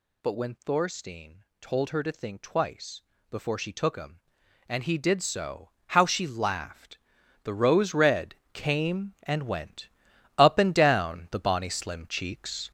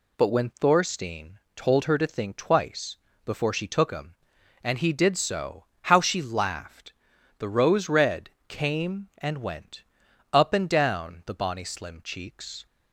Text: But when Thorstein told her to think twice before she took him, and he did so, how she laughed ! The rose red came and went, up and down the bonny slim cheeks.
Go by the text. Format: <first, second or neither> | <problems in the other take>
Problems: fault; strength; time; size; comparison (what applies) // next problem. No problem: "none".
second | gets louder; throughout; 7 dB // pauses between "Thorstein" and "told"; slight; at 1.4 s; 0.16 s long; slight in the second // pauses between "twice" and "before"; slight; at 3.0 s; 0.28 s long; slight in the second // pauses between "red" and "came"; slight; at 8.3 s; 0.18 s long; slight in the second